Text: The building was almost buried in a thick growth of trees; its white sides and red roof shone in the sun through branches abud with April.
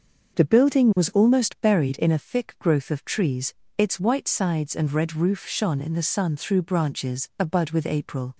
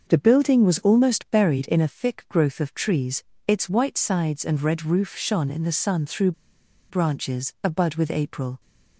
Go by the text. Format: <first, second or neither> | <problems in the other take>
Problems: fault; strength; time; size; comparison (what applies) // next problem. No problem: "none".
first | starts louder than the rest; until 1.1 s; 6.5 dB; also in the first // pauses between "through" and "branches"; noticeable; at 6.3 s; 0.58 s long